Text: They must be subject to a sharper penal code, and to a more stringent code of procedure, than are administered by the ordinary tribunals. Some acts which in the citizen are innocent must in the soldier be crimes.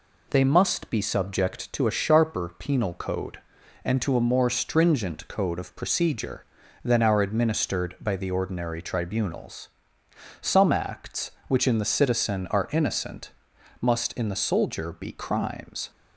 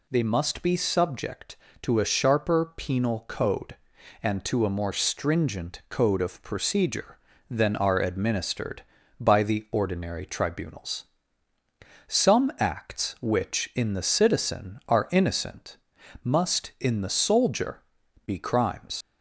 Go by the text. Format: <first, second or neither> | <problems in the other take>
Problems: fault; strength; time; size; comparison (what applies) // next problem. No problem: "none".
first | pauses between "innocent" and "must"; noticeable; at 15.7 s; 0.46 s long; noticeable in the first // pauses between "soldier" and "be"; at 17.8 s; 0.44 s long // leaves "crimes" unfinished; at 19.0 s; 85 ms